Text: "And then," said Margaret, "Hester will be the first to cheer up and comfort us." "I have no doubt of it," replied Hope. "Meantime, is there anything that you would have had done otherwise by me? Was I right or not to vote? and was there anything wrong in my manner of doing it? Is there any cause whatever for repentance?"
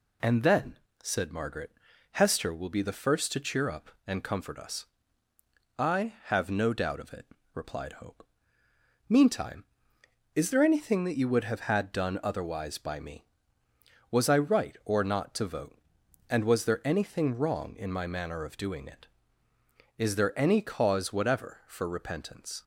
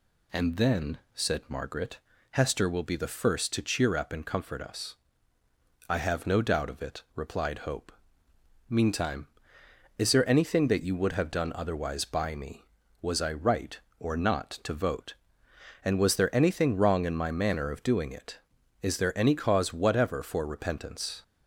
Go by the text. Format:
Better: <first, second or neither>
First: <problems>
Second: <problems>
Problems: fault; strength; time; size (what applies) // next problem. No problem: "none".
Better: first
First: none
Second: skips "had"; at 11.3 s